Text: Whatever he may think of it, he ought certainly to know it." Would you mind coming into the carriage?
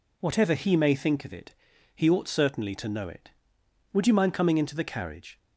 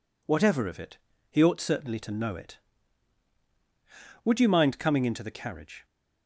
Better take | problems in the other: first | skips "he may think"; at 0.6 s

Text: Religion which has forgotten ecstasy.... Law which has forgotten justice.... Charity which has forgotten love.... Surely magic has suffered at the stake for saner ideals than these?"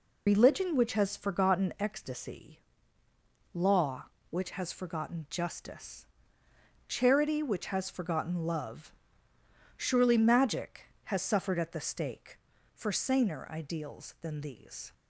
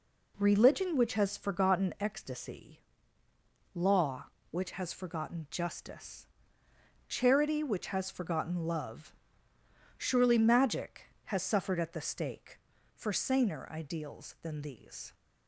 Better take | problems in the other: second | loses the start of "Religion"; at 0.2 s; 130 ms

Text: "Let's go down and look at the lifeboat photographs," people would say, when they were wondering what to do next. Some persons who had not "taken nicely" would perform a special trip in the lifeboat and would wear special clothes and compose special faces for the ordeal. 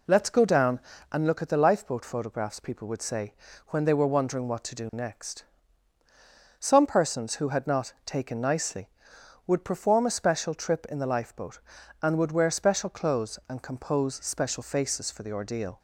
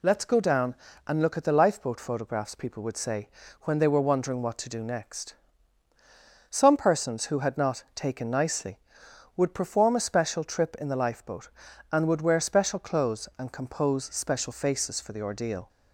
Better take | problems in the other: second | starts louder than the rest; until 1.3 s; 3.5 dB

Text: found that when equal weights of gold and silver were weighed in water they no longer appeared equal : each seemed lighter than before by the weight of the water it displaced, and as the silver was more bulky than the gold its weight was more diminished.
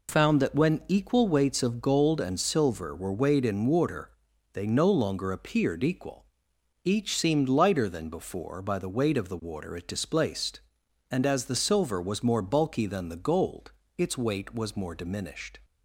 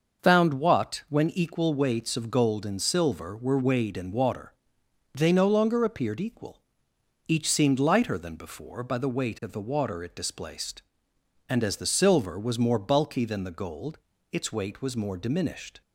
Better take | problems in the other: first | starts louder than the rest; noticeable; until 1.2 s; 6 dB // says "what" for "that"; at 0.5 s // pauses between "water" and "they"; noticeable; at 4.5 s; 0.62 s long; also in the first // pauses between "gold" and "its"; slight; at 13.9 s; 0.34 s long; slight in the first

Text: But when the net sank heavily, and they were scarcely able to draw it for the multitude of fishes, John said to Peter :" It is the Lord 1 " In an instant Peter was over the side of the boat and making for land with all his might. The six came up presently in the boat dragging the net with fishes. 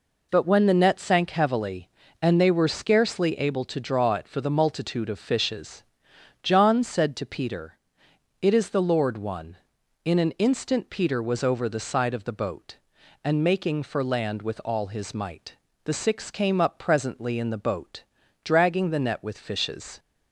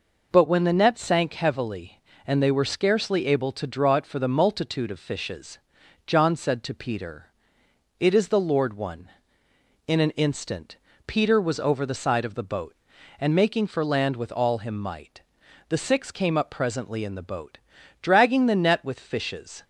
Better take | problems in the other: first | pauses between "instant" and "Peter"; slight; at 10.7 s; 0.28 s long // says "him" for "his"; at 14.5 s // pauses between "boat" and "dragging"; at 17.5 s; 0.42 s long; also in the first

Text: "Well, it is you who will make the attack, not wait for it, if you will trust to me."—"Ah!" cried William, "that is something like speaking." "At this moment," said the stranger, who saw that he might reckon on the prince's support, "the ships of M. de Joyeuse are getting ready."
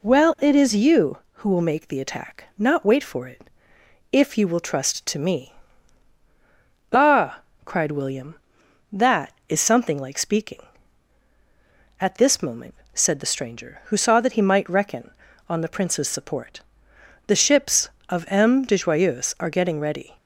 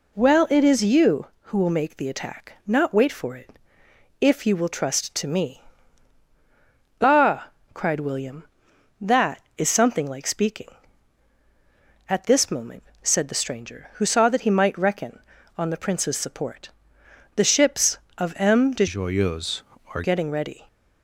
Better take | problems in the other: first | changes voice from "Joyeuse" to "are"; from 18.8 to 20.0 s; 1.2 s long

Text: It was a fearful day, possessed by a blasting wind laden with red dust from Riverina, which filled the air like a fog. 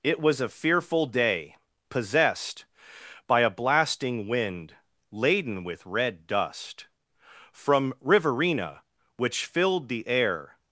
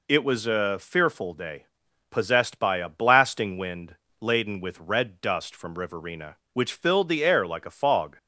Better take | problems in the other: second | pauses between "wind" and "laden"; slight; at 4.7 s; 0.36 s long; slight in the second // stops before "like a fog"; at 10.5 s

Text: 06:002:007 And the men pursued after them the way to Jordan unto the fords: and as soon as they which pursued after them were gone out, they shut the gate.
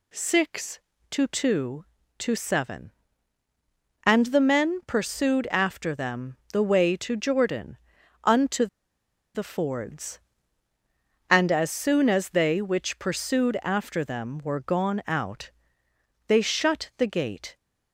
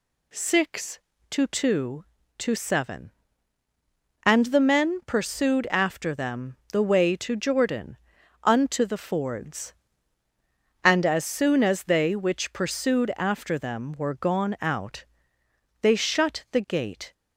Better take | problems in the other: second | pauses between "them" and "the"; slight; at 6.3 s; 0.16 s long; slight in the second // pauses between "Jordan" and "unto"; at 7.7 s; 0.44 s long; also in the second // pauses between "unto" and "the"; noticeable; at 8.6 s; 0.68 s long

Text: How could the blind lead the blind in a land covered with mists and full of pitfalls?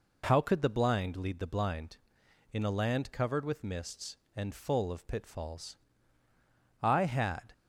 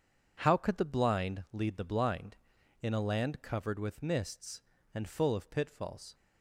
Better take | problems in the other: second | goes on to say "I had"; noticeable; from 6.8 s on; 0.70 s long

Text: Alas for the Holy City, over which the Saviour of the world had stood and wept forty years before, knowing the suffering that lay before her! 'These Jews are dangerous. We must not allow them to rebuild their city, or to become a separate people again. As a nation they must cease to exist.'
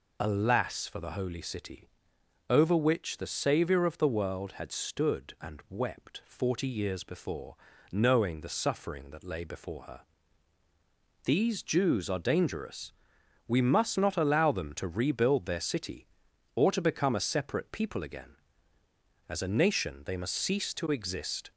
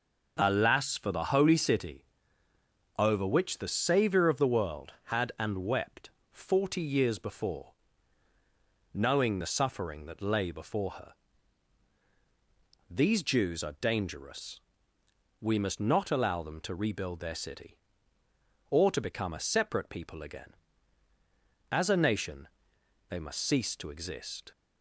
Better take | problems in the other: first | skips "stood"; at 5.3 s // pauses between "wept" and "forty"; slight; at 6.0 s; 0.20 s long // pauses between "nation" and "they"; noticeable; at 22.4 s; 0.62 s long

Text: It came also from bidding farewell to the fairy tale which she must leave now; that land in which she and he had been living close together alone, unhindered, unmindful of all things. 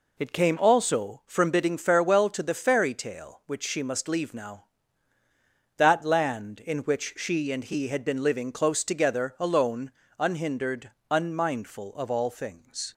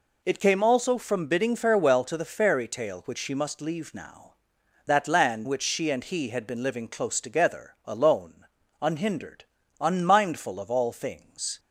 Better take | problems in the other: first | skips "in"; at 5.4 s

